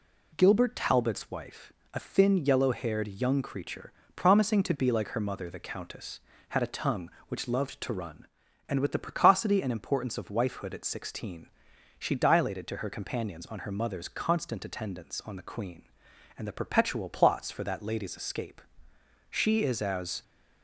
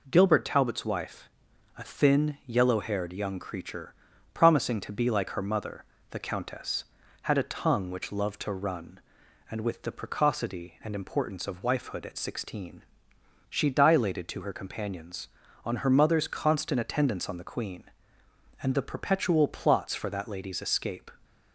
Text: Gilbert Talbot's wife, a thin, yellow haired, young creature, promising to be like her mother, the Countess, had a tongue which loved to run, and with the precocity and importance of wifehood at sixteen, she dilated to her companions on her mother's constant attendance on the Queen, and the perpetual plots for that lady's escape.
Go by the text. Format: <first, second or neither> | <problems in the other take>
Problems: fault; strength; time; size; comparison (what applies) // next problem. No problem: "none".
second | goes on to say "She is as"; noticeable; from 19.3 s on; 0.92 s long